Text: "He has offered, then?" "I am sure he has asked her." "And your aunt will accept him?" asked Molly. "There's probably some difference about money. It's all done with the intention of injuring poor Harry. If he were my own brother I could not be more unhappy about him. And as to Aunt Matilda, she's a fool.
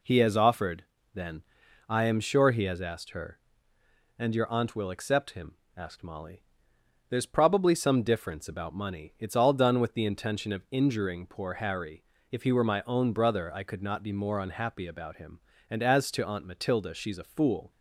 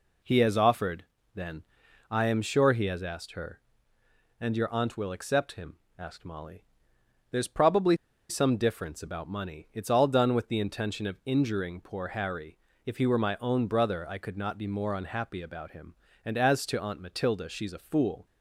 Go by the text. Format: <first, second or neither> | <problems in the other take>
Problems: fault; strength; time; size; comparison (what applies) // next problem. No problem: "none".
first | pauses between "probably" and "some"; slight; at 7.9 s; 0.32 s long